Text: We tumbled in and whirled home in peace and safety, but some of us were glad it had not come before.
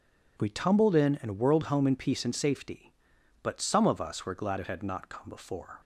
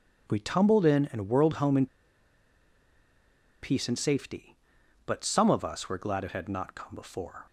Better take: first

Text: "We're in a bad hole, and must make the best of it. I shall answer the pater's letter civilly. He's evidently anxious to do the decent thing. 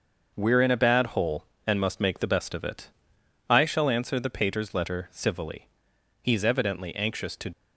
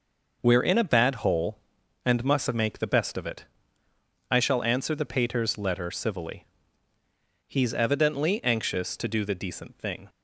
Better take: second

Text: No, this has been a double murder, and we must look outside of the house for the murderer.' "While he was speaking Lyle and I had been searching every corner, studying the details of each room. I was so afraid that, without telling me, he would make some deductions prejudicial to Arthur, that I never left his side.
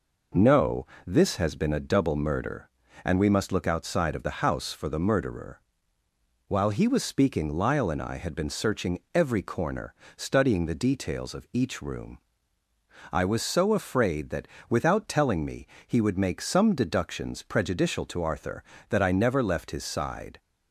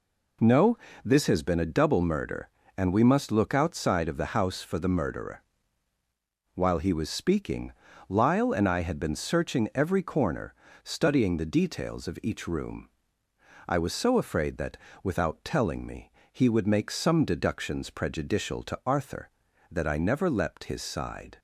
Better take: first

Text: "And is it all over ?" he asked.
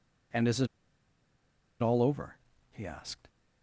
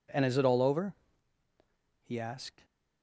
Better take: second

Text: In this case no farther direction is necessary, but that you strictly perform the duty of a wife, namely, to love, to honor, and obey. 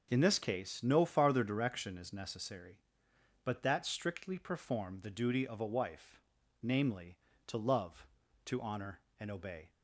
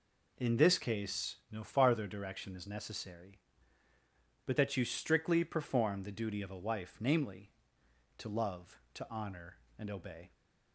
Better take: second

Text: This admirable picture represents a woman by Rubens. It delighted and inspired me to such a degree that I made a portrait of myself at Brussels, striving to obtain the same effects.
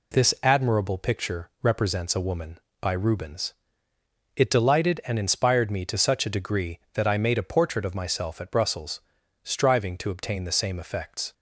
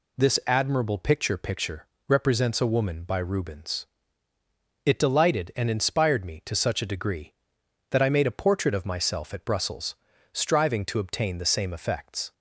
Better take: first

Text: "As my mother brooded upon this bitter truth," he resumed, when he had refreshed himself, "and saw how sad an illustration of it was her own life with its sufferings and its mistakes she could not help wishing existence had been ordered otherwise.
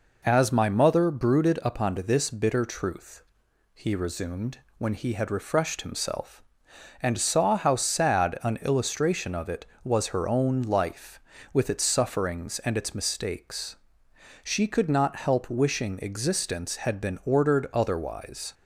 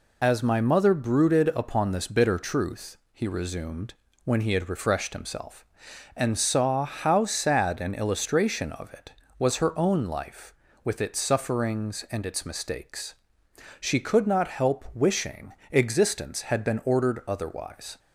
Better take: first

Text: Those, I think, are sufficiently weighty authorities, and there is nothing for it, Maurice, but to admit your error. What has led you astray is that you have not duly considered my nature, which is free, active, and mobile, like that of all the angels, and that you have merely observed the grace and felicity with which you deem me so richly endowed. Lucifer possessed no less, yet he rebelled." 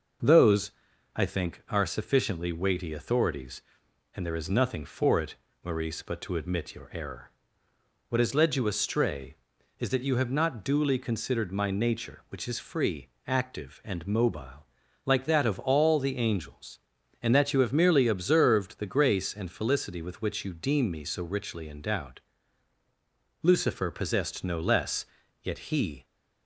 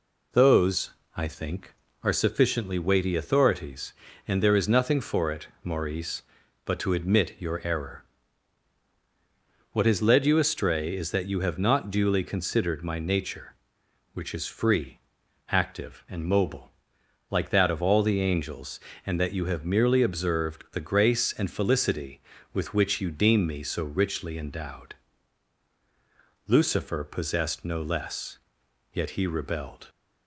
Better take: second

